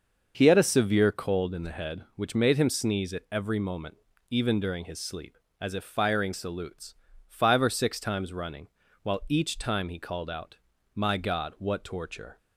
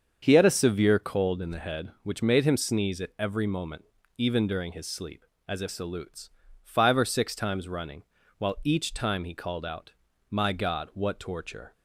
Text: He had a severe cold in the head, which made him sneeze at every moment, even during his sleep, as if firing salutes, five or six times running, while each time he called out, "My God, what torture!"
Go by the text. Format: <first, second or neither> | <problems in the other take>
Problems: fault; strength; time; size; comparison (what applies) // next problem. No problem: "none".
first | starts louder than the rest; until 1.2 s; 7 dB; noticeable in the first // skips "firing"; at 5.6 s